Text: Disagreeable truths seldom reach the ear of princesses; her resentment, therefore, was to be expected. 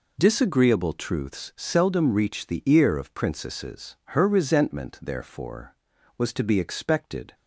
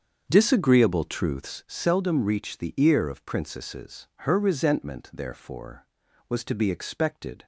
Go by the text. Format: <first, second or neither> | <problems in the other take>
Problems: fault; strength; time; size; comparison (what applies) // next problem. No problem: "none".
first | starts louder than the rest; until 1.6 s; 7 dB